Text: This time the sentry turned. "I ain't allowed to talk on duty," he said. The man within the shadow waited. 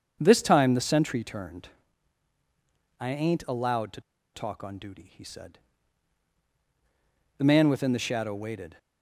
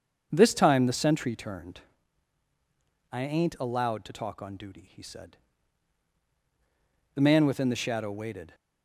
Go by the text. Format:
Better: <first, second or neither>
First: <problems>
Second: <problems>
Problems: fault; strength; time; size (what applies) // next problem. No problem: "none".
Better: second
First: starts louder than the rest; until 1.2 s; 7 dB // pauses between "to" and "talk"; slight; at 4.0 s; 0.34 s long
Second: starts louder than the rest; until 1.3 s; 7 dB